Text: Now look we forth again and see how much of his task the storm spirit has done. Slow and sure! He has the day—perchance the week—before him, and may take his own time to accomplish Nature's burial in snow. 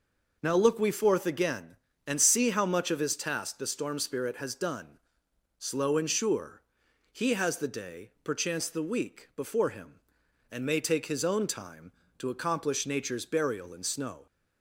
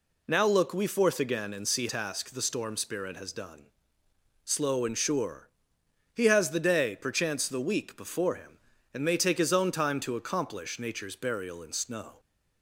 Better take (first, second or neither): first